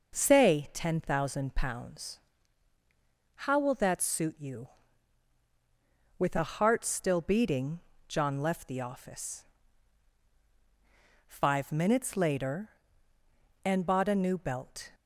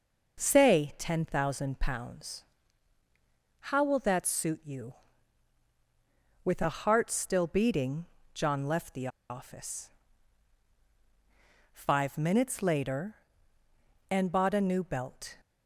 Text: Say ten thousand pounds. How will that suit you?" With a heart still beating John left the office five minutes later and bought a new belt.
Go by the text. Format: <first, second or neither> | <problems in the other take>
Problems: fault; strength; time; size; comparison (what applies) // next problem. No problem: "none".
first | pauses between "beating" and "John"; slight; at 8.0 s; 0.28 s long; slight in the first // pauses between "the" and "office"; slight; at 9.0 s; 0.21 s long // pauses between "office" and "five"; strong; at 9.9 s; 1.8 s long; strong in the first